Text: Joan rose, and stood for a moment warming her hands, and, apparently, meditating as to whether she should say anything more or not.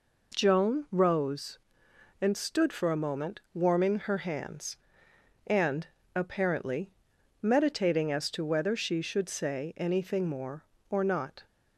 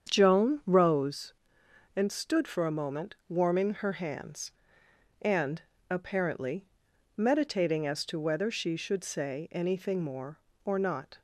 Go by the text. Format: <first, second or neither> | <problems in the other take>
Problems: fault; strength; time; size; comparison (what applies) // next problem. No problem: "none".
first | starts louder than the rest; strong; until 1.3 s; 8 dB